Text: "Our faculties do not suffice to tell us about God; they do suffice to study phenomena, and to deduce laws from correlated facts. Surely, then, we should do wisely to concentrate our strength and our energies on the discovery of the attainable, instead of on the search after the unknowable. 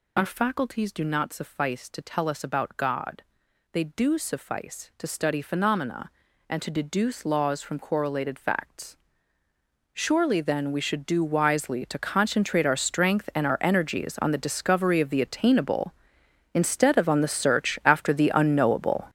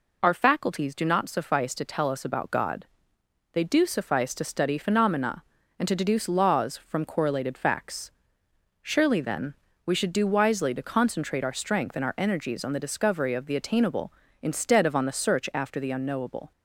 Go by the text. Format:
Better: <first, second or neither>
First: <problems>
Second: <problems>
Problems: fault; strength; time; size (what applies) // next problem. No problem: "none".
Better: second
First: gets louder; strong; throughout; 10.5 dB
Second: none